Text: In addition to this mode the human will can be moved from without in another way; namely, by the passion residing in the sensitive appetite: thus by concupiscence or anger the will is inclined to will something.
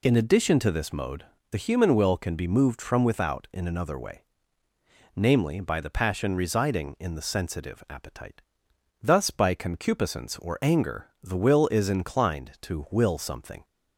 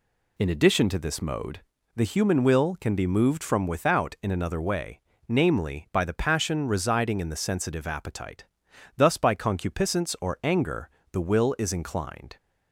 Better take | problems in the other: first | pauses between "mode" and "the"; slight; at 1.6 s; 0.34 s long; slight in the first // pauses between "anger" and "the"; slight; at 10.9 s; 0.22 s long; slight in the first // stops before "to will something"; at 12.3 s

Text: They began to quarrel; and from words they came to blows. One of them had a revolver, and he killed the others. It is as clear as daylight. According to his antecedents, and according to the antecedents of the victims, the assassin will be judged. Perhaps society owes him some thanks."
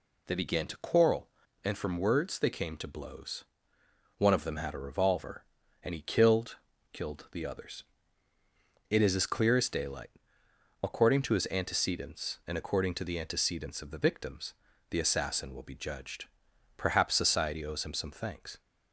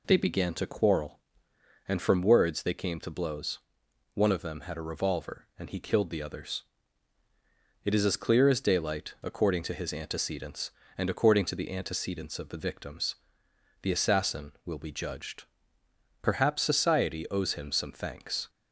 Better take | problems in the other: second | says "killed" twice; at 6.9 s

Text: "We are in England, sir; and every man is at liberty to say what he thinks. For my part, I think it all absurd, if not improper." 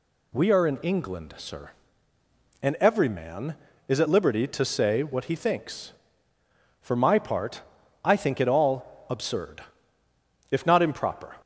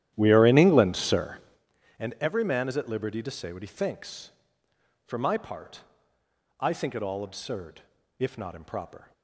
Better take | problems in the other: first | starts louder than the rest; strong; until 1.7 s; 11.5 dB

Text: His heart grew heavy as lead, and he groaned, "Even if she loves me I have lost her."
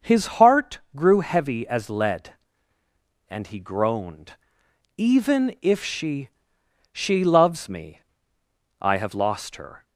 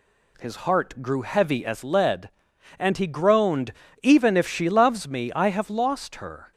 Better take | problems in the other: second | pauses between "heart" and "grew"; slight; at 0.7 s; 0.16 s long // says "she" twice; at 6.9 s // pauses between "me" and "I"; noticeable; at 7.9 s; 0.80 s long

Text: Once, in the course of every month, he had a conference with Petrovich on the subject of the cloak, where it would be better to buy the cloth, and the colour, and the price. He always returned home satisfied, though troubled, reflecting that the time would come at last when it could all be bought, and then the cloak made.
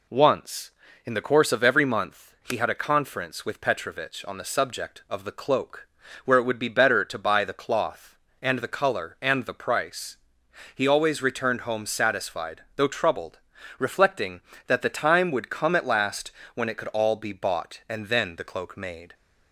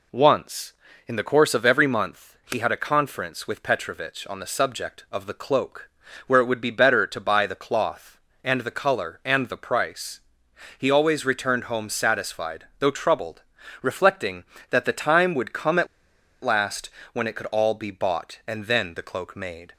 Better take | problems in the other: first | pauses between "at" and "last"; noticeable; at 15.8 s; 0.57 s long // pauses between "last" and "when"; slight; at 16.8 s; 0.22 s long; slight in the first

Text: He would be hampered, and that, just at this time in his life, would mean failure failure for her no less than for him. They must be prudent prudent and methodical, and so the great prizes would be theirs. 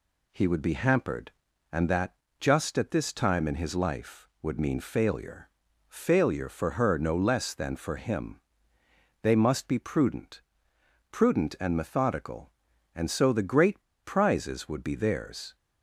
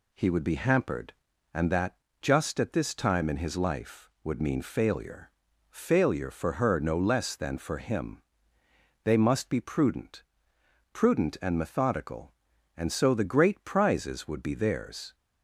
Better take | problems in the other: second | pauses between "failure" and "failure"; at 5.4 s; 0.38 s long; also in the second // pauses between "prudent" and "prudent"; noticeable; at 10.4 s; 0.68 s long; noticeable in the second // pauses between "great" and "prizes"; slight; at 13.8 s; 0.22 s long

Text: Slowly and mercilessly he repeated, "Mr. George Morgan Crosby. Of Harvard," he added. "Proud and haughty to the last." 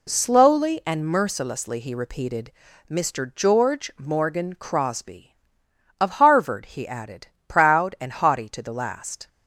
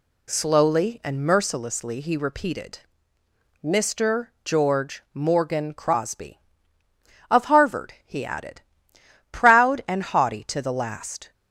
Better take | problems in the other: neither | none

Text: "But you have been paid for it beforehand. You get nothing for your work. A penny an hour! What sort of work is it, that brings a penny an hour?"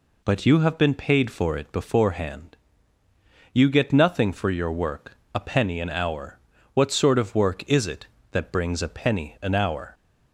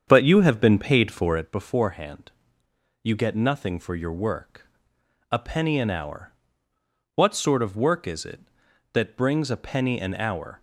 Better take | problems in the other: first | starts louder than the rest; strong; until 1.6 s; 7.5 dB

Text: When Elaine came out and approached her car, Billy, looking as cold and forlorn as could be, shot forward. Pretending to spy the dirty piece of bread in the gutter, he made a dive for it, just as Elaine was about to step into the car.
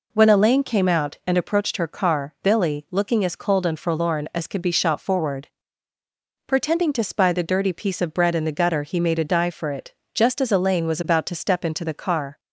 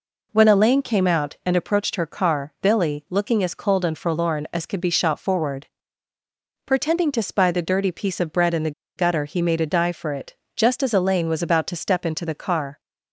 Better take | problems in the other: first | pauses between "the" and "gutter"; slight; at 8.7 s; 0.25 s long

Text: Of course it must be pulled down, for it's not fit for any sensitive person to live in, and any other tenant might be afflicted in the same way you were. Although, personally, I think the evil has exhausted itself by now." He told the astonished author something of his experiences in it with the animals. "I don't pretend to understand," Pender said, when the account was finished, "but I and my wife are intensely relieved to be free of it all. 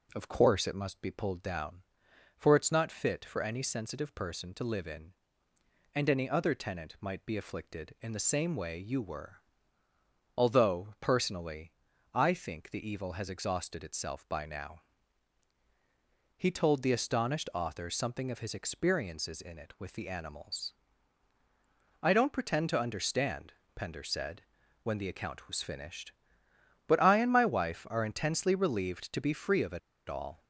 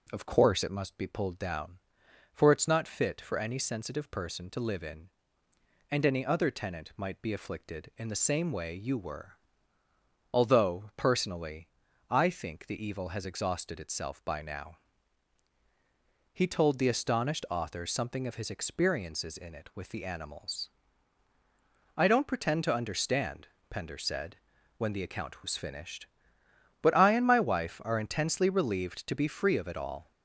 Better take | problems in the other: second | pauses between "it" and "all"; slight; at 29.7 s; 0.29 s long

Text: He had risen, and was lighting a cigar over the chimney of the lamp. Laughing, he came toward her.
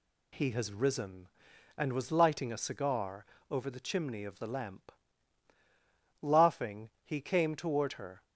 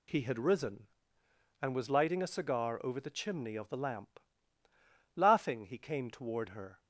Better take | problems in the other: second | says "has" for "had"; at 0.4 s // pauses between "cigar" and "over"; slight; at 3.2 s; 0.28 s long

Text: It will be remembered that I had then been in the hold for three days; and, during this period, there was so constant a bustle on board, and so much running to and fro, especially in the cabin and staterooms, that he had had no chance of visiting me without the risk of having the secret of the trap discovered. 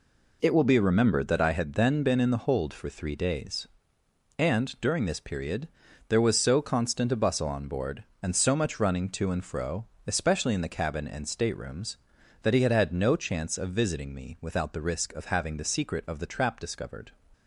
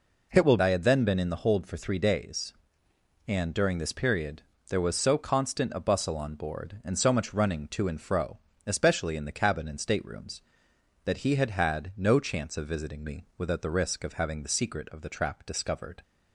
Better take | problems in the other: first | skips "be remembered that"; at 0.5 s

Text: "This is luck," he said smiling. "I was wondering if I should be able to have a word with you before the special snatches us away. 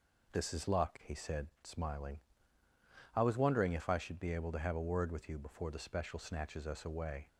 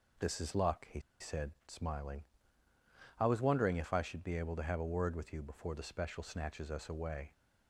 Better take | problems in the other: first | pauses between "he" and "said"; slight; at 0.9 s; 0.21 s long

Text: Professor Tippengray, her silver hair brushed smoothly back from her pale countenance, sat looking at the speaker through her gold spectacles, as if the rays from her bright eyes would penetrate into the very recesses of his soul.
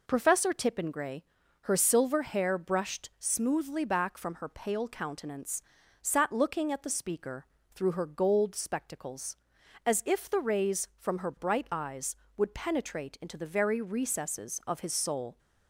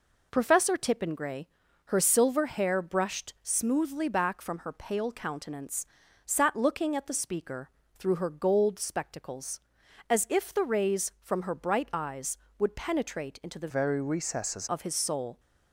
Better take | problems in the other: first | pauses between "speaker" and "through"; slight; at 7.6 s; 0.28 s long; slight in the first // changes voice from "very" to "recesses"; from 13.6 to 14.6 s; 1.0 s long

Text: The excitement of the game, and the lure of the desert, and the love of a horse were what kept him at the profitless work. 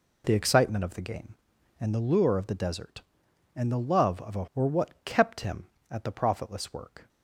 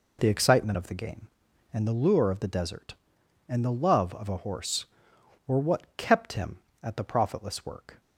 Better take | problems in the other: second | skips "horse"; at 4.4 s

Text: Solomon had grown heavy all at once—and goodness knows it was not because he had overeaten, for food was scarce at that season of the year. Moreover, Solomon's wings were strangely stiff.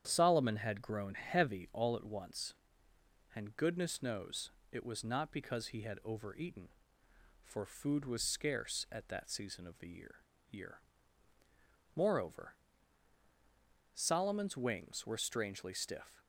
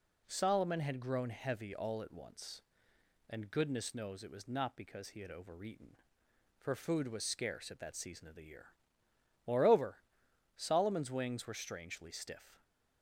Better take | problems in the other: second | starts louder than the rest; strong; until 1.0 s; 9 dB // pauses between "knows" and "it"; slight; at 4.4 s; 0.22 s long // says "year" twice; at 10.4 s

